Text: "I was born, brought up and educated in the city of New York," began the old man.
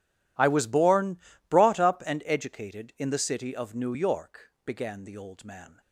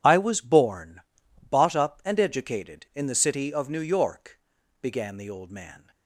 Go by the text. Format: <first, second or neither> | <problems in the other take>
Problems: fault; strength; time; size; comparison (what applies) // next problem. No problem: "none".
first | says "bought" for "brought"; at 1.5 s